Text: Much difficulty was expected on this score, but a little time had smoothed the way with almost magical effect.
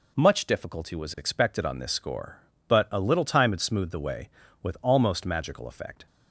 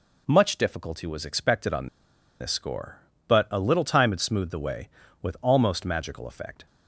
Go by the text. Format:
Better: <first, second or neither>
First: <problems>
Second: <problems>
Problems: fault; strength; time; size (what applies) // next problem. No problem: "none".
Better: first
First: none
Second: pauses between "on" and "this"; noticeable; at 1.8 s; 0.54 s long